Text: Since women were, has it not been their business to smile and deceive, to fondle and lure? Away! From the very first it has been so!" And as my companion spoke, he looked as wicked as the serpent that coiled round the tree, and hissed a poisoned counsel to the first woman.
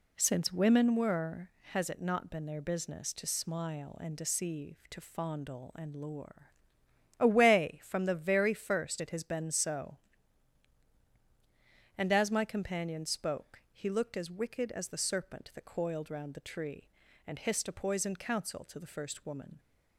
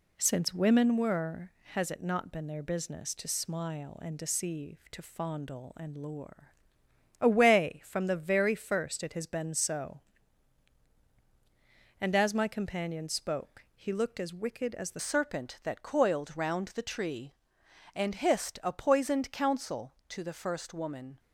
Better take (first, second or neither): first